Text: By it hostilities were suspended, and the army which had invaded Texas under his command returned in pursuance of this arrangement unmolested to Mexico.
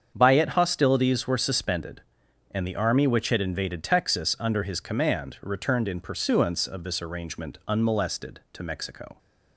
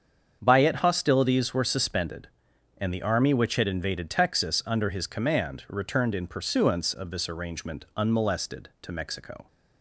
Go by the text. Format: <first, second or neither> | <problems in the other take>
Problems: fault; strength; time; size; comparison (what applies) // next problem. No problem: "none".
neither | starts louder than the rest; strong; the same in both